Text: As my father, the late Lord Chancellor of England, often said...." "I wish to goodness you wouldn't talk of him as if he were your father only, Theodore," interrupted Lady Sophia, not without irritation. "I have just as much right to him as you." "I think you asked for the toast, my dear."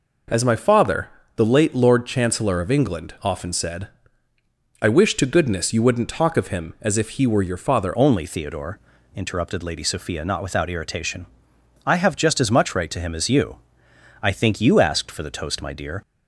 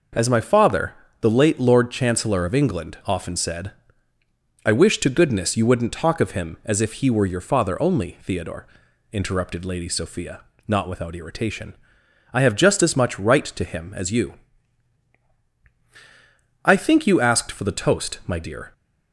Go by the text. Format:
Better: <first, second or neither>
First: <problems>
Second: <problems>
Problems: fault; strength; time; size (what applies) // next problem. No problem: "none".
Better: second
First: changes voice at "only"; from 7.9 s on; 8.1 s long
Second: none